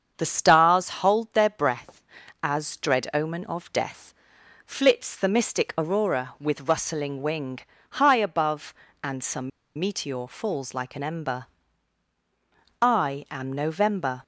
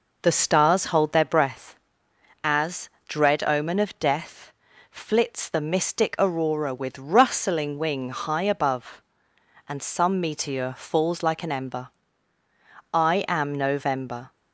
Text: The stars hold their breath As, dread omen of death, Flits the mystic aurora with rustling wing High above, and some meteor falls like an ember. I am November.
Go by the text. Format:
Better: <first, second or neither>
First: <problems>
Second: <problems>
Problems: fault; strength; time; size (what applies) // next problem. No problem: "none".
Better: second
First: starts louder than the rest; strong; until 1.2 s; 7 dB // pauses between "wing" and "High"; slight; at 7.5 s; 0.32 s long // pauses between "some" and "meteor"; slight; at 9.5 s; 0.28 s long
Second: none